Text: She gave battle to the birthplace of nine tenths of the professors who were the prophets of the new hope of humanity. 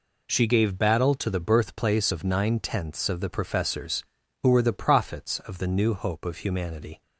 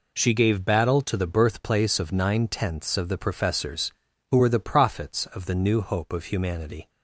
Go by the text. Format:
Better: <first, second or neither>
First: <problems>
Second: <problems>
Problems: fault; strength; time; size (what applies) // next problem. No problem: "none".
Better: neither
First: none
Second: none